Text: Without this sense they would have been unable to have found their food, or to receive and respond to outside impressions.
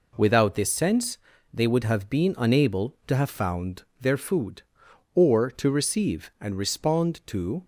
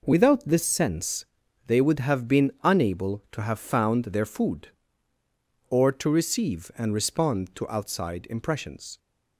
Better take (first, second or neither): second